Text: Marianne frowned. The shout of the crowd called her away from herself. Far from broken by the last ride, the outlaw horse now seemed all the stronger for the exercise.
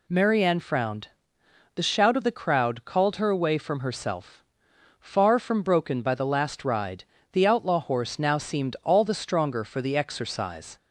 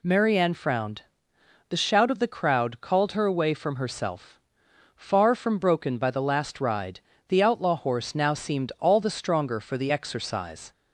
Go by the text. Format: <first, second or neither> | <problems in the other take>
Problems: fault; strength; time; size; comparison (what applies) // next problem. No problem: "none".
neither | none